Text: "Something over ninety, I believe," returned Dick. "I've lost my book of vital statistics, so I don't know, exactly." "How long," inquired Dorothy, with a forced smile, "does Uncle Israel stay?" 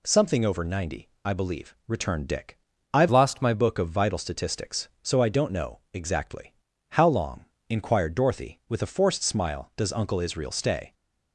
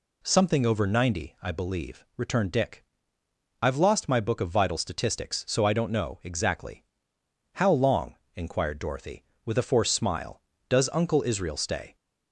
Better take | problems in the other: second | changes voice from "lost" to "my"; from 3.1 to 3.5 s; 0.4 s long

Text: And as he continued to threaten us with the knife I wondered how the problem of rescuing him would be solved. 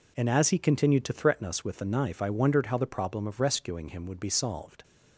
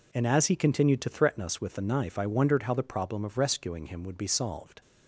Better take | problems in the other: neither | none

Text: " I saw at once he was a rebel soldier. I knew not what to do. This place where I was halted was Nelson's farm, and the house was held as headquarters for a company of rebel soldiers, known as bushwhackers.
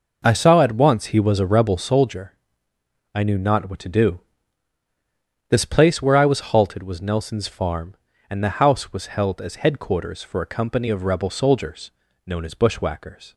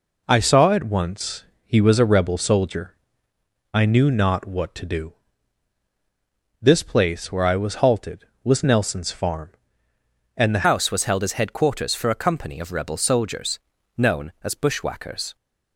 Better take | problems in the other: first | pauses between "once" and "he"; slight; at 1.4 s; 0.22 s long // changes voice at "house"; from 10.6 s on; 4.7 s long

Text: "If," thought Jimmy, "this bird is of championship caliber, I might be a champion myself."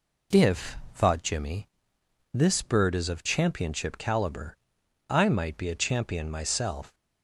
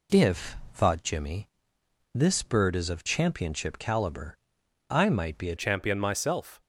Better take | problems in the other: first | changes voice at "champion"; from 5.5 s on; 1.0 s long

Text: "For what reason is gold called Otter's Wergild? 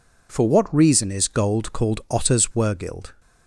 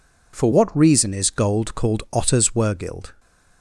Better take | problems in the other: neither | none

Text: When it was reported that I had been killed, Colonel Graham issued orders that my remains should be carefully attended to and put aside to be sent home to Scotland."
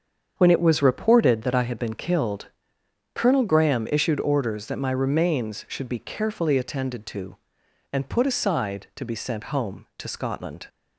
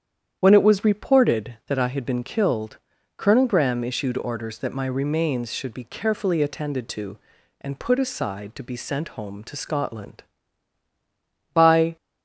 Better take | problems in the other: first | starts louder than the rest; strong; until 1.4 s; 9 dB; strong in the first // goes on to say "By"; slight; from 11.5 s on; 0.42 s long

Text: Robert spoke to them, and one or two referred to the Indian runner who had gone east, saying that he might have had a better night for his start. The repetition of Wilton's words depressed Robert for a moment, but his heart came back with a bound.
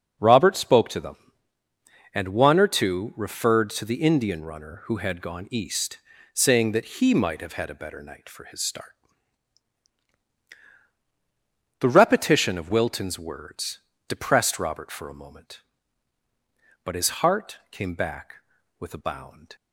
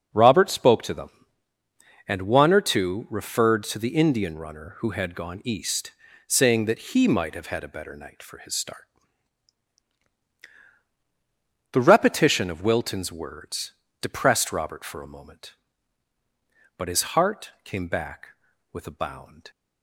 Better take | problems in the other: neither | pauses between "words" and "depressed"; slight; the same in both

